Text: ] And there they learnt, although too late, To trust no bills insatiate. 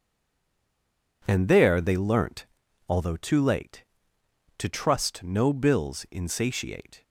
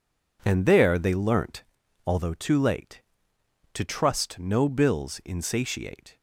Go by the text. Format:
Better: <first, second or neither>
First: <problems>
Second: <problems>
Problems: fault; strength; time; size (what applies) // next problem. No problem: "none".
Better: second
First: stays silent before the first word; noticeable; until 1.2 s; 1.2 s long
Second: none